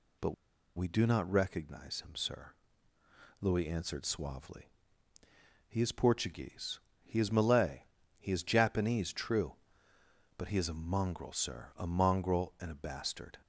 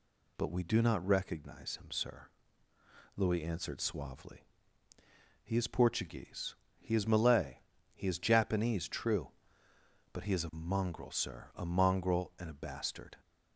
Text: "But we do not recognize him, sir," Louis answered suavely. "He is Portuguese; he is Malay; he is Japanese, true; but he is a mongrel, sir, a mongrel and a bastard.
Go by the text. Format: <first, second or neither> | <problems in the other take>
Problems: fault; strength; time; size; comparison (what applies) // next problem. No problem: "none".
second | pauses between "But" and "we"; at 0.3 s; 0.41 s long